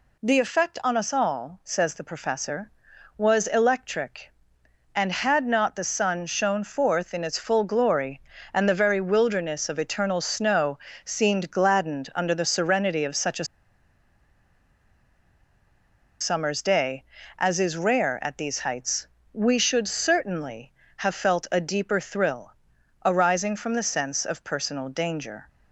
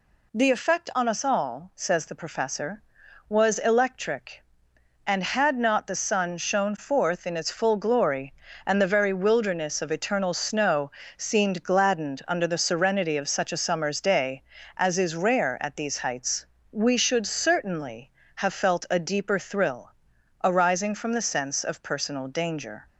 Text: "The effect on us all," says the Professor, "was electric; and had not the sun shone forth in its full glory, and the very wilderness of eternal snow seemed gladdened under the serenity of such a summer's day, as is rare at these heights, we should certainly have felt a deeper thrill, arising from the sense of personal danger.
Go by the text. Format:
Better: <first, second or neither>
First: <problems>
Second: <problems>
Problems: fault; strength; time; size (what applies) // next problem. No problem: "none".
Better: second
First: pauses between "snow" and "seemed"; slight; at 10.7 s; 0.24 s long // pauses between "a" and "summer's"; strong; at 13.4 s; 2.7 s long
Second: pauses between "snow" and "seemed"; slight; at 10.9 s; 0.24 s long